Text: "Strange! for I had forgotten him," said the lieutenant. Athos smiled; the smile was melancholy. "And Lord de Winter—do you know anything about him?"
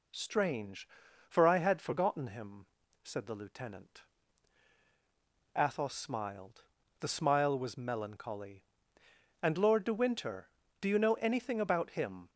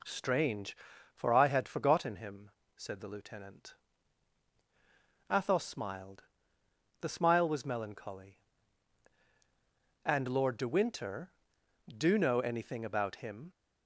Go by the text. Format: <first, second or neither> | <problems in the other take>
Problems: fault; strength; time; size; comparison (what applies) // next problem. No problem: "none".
first | skips "you"; at 12.1 s